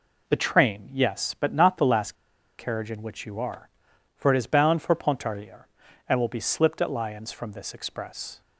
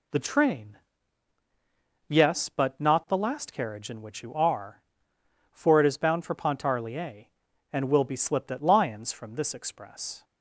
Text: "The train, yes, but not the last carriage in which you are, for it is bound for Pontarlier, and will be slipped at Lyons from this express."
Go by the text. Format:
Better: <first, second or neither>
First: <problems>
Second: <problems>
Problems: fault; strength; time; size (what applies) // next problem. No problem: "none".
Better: second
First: pauses between "last" and "carriage"; at 2.1 s; 0.43 s long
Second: none